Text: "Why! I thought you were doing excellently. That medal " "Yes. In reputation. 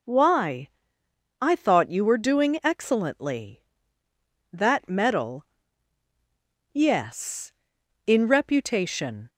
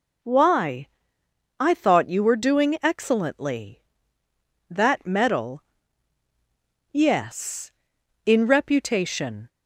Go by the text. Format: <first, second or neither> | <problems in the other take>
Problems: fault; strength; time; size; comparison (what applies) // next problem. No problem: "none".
neither | none